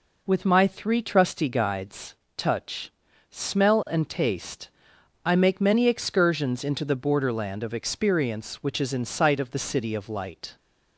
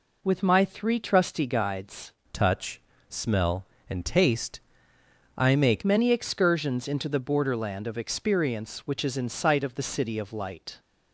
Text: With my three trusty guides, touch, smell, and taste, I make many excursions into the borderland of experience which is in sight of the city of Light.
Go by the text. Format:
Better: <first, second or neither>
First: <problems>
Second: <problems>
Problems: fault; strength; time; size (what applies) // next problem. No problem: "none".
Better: first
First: none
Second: changes voice from "touch" to "make"; from 2.3 to 5.8 s; 3.5 s long